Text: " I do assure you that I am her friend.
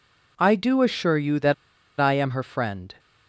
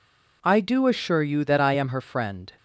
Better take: second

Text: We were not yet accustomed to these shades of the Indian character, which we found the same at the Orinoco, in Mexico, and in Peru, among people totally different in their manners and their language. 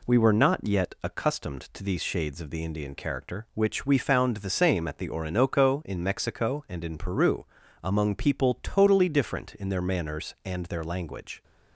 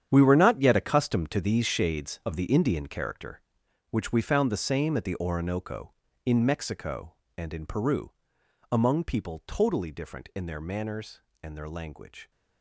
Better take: first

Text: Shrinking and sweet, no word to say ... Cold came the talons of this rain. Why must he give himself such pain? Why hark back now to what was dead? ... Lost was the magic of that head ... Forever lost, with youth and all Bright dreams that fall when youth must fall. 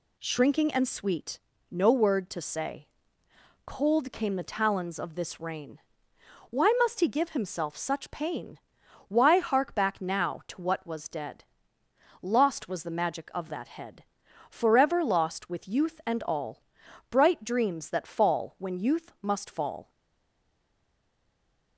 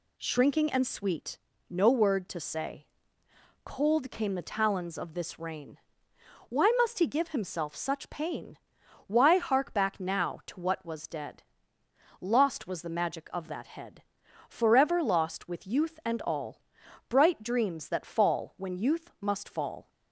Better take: second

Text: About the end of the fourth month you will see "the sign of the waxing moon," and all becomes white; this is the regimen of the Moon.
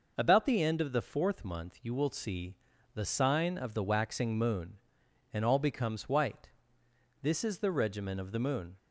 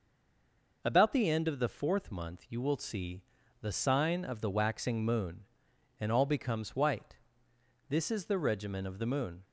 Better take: first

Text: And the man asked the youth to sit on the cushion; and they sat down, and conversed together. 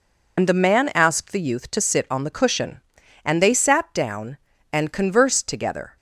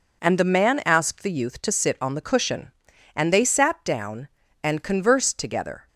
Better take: second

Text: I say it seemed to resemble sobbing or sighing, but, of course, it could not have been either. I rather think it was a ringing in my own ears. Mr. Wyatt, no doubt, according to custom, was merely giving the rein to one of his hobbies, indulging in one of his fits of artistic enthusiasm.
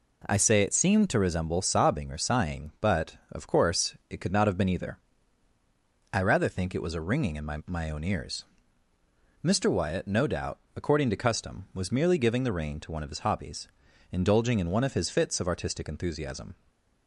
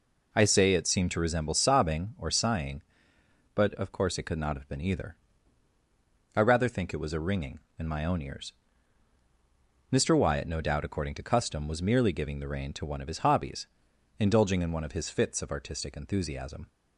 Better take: second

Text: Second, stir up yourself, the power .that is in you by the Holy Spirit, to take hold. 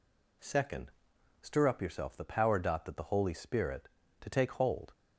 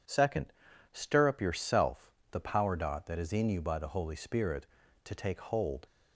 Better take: second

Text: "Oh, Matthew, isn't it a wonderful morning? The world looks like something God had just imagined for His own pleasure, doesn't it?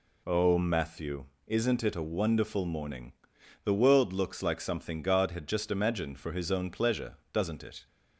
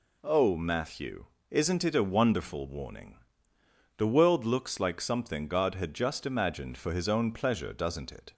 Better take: first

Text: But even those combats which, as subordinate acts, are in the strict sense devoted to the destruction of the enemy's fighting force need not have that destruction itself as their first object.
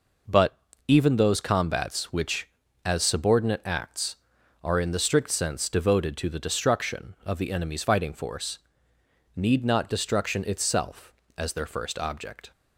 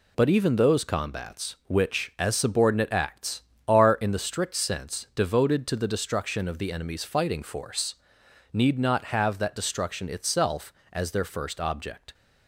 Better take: second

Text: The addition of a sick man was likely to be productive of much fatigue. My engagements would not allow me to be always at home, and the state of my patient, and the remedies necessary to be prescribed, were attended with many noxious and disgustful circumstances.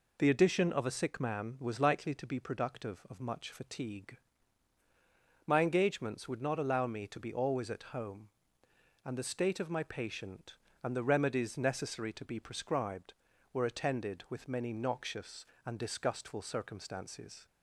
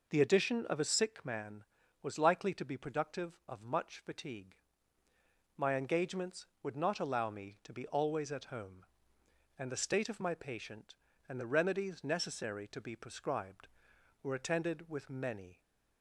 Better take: first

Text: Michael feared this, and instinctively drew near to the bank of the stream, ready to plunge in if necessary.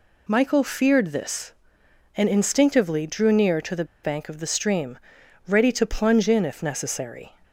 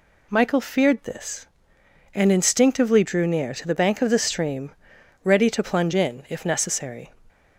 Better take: second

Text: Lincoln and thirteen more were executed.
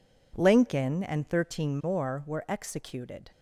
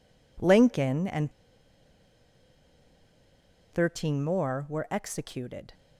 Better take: first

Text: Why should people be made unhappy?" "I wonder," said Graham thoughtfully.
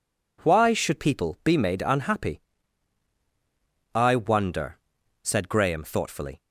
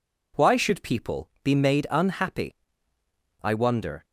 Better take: first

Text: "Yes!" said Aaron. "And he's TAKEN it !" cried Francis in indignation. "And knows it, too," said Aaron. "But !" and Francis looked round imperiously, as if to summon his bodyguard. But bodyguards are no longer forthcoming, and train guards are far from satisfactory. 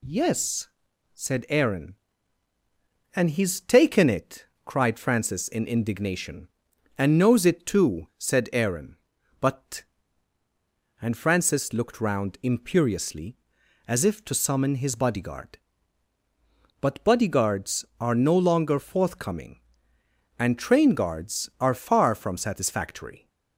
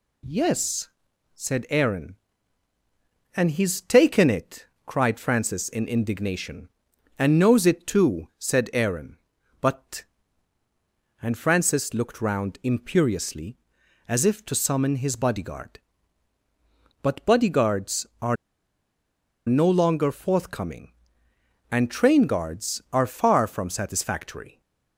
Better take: first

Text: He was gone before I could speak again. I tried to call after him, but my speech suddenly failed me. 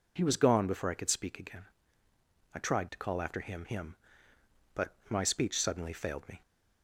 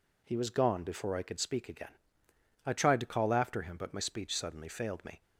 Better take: second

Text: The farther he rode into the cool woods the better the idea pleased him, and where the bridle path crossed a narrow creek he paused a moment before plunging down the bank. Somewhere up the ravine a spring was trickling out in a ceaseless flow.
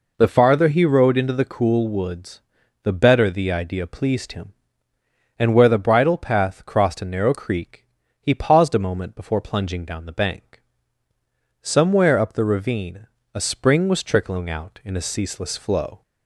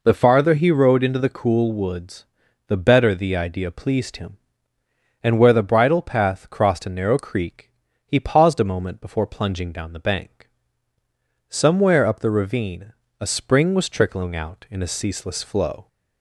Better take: neither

